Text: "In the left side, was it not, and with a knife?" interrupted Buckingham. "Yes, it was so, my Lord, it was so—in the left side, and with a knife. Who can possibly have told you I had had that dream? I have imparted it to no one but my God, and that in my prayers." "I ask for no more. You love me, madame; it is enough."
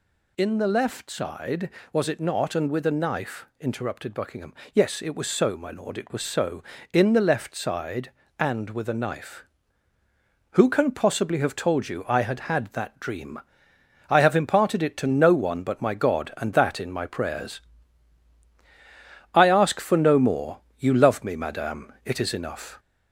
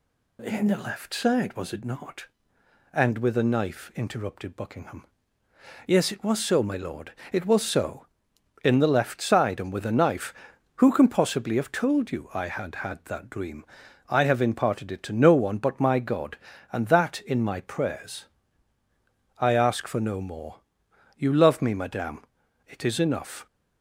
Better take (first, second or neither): second